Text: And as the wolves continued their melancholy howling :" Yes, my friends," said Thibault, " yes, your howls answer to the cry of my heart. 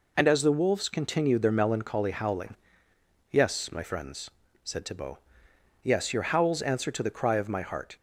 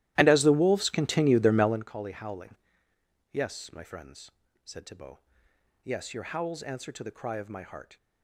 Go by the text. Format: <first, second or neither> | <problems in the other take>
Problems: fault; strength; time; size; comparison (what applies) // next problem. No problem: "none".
first | starts louder than the rest; strong; until 1.9 s; 15 dB